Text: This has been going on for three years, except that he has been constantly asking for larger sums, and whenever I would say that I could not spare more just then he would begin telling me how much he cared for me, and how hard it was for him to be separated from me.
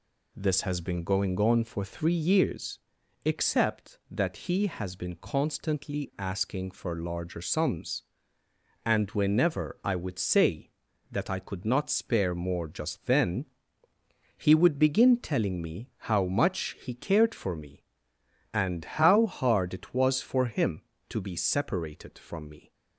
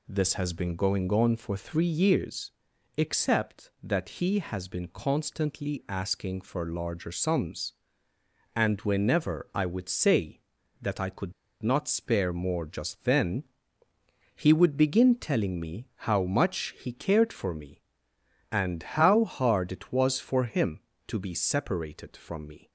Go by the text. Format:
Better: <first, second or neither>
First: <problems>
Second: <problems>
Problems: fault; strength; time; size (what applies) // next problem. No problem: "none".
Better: first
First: pauses between "then" and "he"; noticeable; at 13.4 s; 0.90 s long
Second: pauses between "could" and "not"; slight; at 11.3 s; 0.30 s long // pauses between "then" and "he"; noticeable; at 13.4 s; 0.90 s long